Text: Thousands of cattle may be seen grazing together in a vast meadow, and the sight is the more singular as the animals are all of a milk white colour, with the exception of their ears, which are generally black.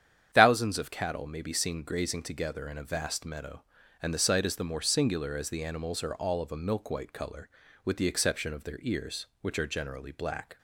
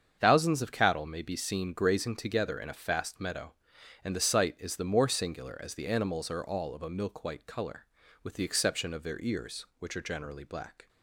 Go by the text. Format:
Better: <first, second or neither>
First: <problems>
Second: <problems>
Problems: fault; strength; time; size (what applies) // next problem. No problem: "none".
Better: first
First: starts louder than the rest; strong; until 1.3 s; 9 dB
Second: starts louder than the rest; strong; until 1.2 s; 7.5 dB // says "fast" for "vast"; at 2.7 s